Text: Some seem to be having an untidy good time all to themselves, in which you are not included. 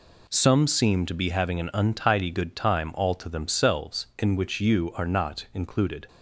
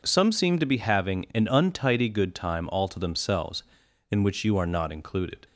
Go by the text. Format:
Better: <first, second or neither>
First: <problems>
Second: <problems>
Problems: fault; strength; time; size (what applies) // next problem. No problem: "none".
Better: neither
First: none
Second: none